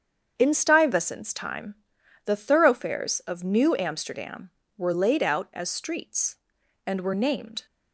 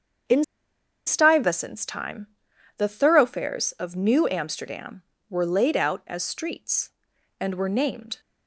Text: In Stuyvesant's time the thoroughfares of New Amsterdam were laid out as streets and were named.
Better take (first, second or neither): first